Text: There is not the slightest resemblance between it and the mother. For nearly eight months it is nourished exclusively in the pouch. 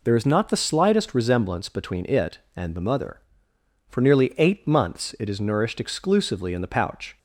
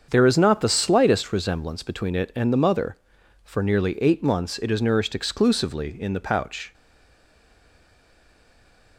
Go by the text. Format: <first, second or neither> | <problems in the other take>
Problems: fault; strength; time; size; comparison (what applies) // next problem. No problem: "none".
first | starts louder than the rest; strong; until 1.1 s; 7 dB // stays silent after the last word; from 6.7 s on; 2.2 s long